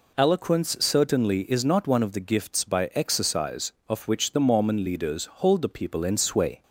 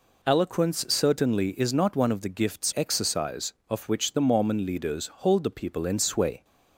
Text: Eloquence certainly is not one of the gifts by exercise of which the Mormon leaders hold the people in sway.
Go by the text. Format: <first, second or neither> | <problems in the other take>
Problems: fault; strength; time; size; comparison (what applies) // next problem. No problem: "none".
first | skips "by"; at 2.7 s // pauses between "leaders" and "hold"; slight; at 5.0 s; 0.16 s long; slight in the first